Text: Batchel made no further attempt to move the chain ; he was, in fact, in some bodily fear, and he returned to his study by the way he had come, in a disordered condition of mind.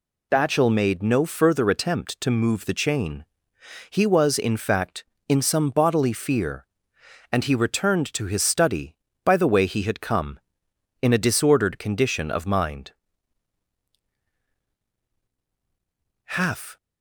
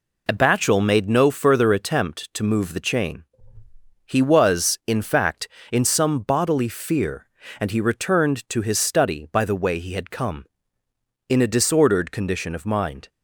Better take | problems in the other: second | goes on to say "Half"; from 16.2 s on; 0.52 s long

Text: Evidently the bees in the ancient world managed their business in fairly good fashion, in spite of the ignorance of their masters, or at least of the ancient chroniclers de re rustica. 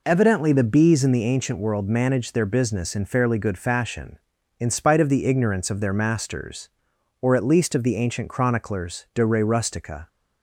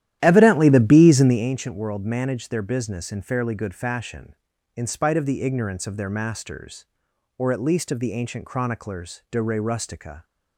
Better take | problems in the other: first | starts louder than the rest; strong; until 1.5 s; 12 dB

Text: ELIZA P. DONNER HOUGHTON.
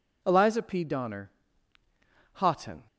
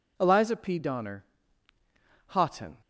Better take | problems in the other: neither | pauses between "DONNER" and "HOUGHTON"; the same in both

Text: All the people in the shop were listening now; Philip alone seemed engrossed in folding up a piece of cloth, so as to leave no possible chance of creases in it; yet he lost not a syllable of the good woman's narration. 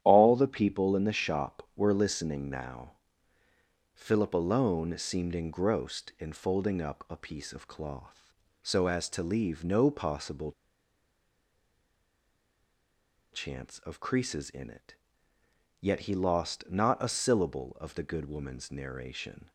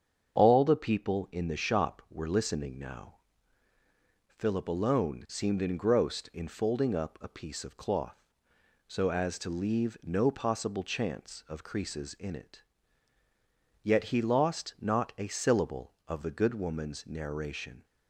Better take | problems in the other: second | starts louder than the rest; strong; until 1.0 s; 11 dB; strong in the second // pauses between "possible" and "chance"; strong; at 10.5 s; 2.8 s long

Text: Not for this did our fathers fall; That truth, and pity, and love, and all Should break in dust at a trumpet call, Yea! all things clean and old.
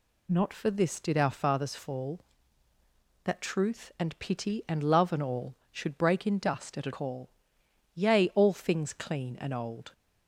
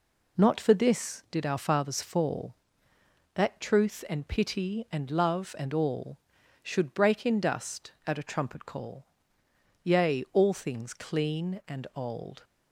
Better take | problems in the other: second | skips "trumpet"; at 6.9 s

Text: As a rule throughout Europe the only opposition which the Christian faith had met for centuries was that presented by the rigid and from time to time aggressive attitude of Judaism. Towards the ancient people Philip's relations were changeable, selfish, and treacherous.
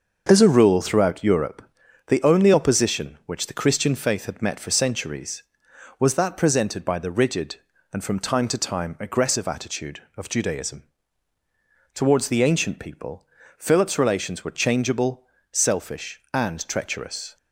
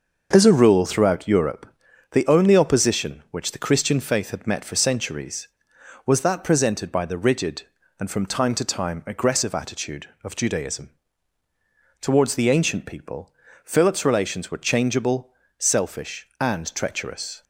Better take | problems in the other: neither | starts louder than the rest; noticeable; the same in both // pauses between "Europe" and "the"; noticeable; the same in both // pauses between "people" and "Philip's"; slight; the same in both

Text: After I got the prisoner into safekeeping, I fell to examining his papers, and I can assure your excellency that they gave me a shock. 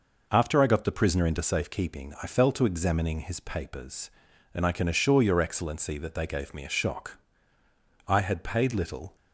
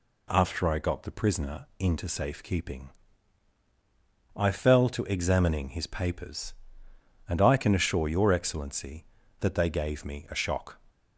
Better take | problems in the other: second | goes on to say "I had paid little"; noticeable; from 8.0 s on; 1.0 s long

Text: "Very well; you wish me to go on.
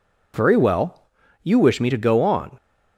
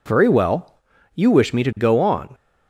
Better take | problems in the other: neither | none

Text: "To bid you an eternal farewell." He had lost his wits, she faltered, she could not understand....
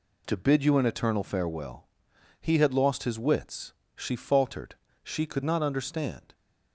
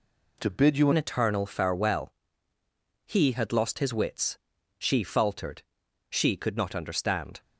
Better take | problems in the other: first | changes voice at "an"; from 0.9 s on; 6.5 s long

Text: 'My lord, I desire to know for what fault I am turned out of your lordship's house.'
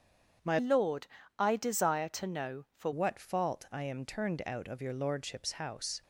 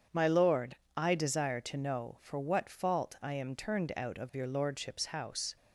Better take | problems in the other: second | starts louder than the rest; strong; until 1.7 s; 7.5 dB; strong in the second // changes voice from "lord" to "for"; from 0.5 to 2.9 s; 2.4 s long

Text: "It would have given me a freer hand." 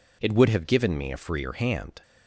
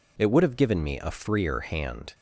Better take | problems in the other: neither | none

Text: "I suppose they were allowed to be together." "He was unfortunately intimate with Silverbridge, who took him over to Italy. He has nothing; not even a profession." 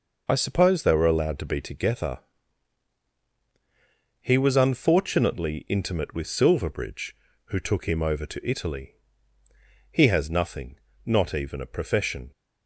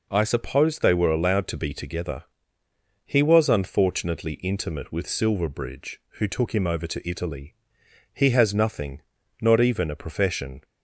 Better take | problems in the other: neither | none

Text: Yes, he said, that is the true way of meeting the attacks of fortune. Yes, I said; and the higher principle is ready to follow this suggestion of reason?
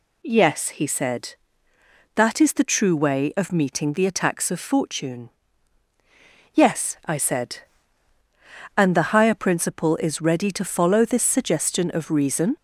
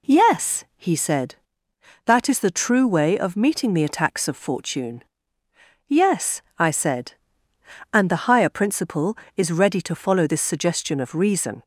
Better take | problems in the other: neither | none

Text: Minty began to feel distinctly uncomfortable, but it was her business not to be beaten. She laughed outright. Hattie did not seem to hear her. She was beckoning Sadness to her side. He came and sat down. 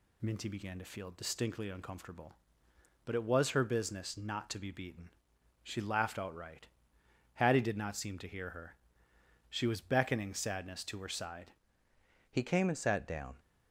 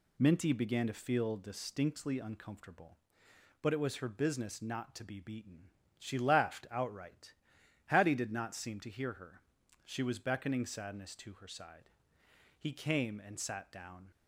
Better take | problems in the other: second | changes voice at "He"; from 12.2 s on; 1.1 s long

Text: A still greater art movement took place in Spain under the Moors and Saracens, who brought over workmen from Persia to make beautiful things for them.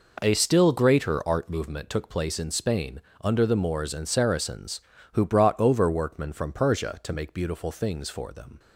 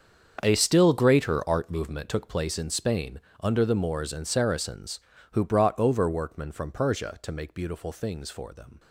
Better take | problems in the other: first | gets quieter; strong; throughout; 14.5 dB // pauses between "Spain" and "under"; slight; at 3.1 s; 0.22 s long; slight in the first

